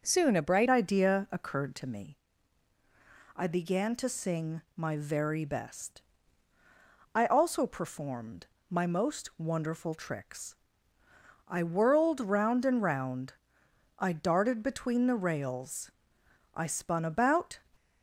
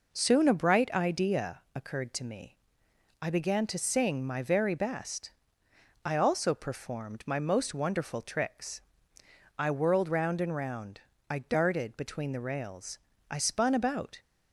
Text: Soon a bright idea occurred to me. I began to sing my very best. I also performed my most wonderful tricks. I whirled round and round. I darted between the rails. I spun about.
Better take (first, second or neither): second